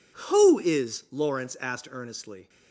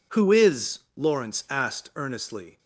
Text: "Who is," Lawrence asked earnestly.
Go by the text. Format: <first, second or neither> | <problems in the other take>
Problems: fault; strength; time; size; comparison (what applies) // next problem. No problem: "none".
neither | none